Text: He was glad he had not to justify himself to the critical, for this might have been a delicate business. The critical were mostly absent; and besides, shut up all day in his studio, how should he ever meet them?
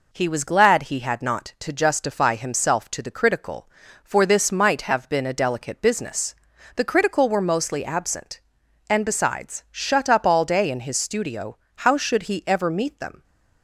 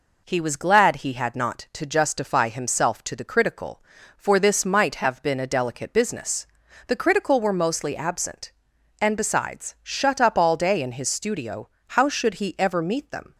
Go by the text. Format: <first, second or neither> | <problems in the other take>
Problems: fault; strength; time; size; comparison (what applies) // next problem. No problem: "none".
neither | none